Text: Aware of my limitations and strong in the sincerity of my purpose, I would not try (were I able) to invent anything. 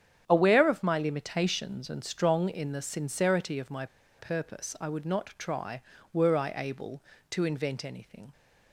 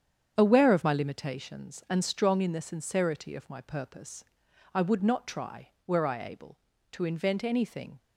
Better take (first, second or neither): second